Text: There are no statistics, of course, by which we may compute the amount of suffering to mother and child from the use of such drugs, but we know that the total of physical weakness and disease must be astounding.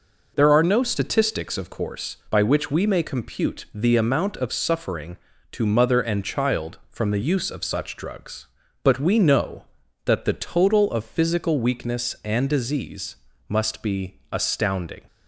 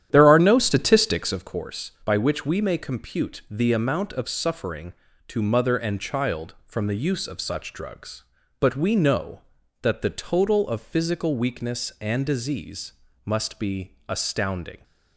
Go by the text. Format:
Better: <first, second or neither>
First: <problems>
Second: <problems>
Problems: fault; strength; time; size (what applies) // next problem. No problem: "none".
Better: first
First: pauses between "disease" and "must"; slight; at 13.1 s; 0.30 s long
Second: starts louder than the rest; strong; until 1.5 s; 10.5 dB // pauses between "disease" and "must"; slight; at 12.9 s; 0.30 s long